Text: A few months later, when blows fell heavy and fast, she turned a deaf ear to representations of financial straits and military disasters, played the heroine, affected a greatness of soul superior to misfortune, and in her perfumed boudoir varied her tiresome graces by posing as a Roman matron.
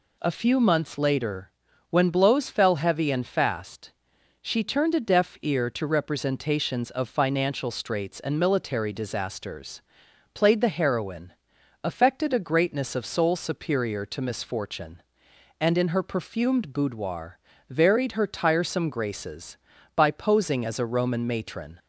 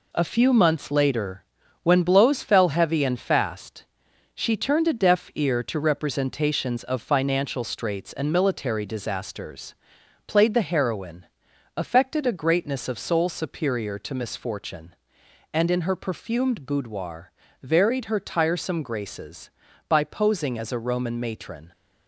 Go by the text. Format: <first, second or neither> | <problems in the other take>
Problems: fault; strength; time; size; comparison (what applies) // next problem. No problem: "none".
first | gets quieter; noticeable; throughout; 6 dB // pauses between "boudoir" and "varied"; slight; at 17.3 s; 0.32 s long; slight in the first